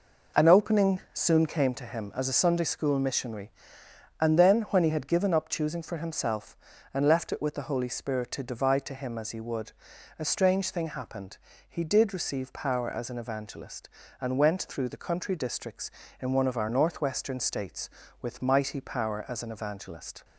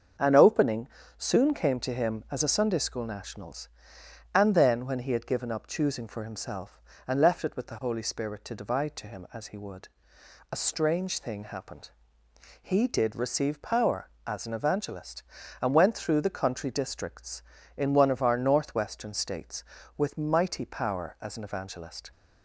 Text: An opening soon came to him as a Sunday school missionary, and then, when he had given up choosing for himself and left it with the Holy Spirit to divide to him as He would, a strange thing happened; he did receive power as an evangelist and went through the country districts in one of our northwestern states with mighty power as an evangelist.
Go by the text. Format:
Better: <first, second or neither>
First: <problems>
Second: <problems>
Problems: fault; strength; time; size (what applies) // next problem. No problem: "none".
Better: first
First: none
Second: starts louder than the rest; until 1.5 s; 6.5 dB // pauses between "opening" and "soon"; slight; at 0.8 s; 0.32 s long // says "nationals" for "missionary"; at 3.0 s